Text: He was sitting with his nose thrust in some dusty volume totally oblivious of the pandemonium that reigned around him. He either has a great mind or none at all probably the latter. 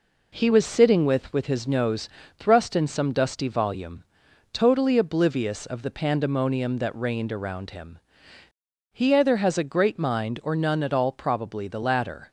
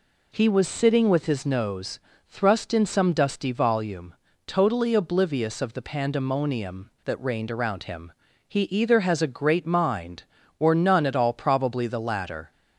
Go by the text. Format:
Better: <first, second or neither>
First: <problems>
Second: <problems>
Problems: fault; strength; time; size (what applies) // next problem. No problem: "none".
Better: second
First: says "with" twice; at 1.3 s // pauses between "nose" and "thrust"; slight; at 2.0 s; 0.30 s long // pauses between "volume" and "totally"; noticeable; at 4.0 s; 0.48 s long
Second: pauses between "nose" and "thrust"; slight; at 1.9 s; 0.30 s long // pauses between "volume" and "totally"; slight; at 4.1 s; 0.32 s long